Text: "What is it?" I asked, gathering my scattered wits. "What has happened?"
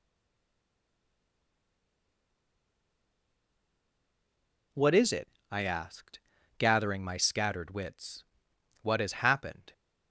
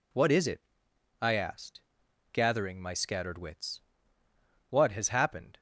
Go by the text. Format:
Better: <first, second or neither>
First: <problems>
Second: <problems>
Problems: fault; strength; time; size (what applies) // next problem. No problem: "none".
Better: second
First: stays silent before the first word; strong; until 4.7 s; 4.7 s long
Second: none